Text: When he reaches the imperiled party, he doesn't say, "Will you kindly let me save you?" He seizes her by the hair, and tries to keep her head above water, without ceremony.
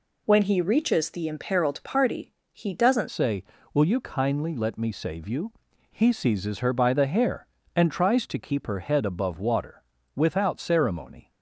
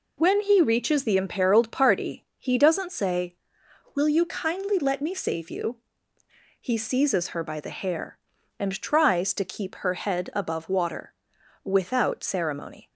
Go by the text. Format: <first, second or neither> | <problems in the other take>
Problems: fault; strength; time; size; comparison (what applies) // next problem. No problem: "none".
second | changes voice at "say"; from 3.1 s on; 8.2 s long